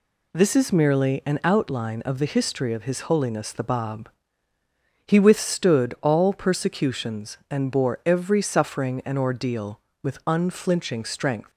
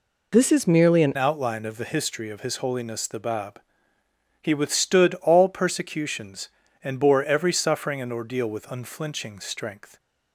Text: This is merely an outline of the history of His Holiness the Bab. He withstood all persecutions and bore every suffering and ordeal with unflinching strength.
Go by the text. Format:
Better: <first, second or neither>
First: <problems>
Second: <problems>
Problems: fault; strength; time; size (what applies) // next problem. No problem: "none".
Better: first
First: none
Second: changes voice at "outline"; from 1.1 s on; 8.8 s long